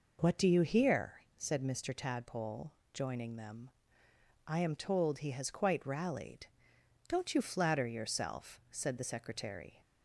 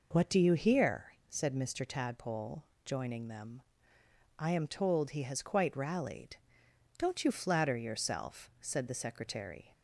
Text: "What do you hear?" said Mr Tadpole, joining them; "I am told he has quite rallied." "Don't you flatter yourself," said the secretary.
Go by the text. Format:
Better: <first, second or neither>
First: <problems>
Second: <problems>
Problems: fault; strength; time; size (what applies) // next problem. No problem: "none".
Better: neither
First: none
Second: none